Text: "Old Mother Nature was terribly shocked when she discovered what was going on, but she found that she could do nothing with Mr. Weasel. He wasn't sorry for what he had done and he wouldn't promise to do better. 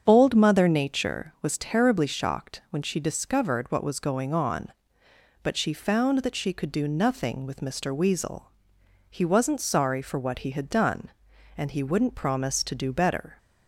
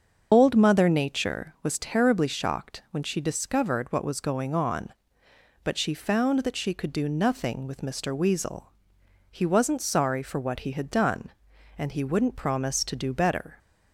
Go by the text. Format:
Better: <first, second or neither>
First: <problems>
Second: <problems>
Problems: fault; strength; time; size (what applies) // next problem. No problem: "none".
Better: first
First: starts louder than the rest; strong; until 1.0 s; 7.5 dB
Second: loses the start of "Old"; at 0.3 s; 35 ms // starts louder than the rest; until 1.3 s; 7 dB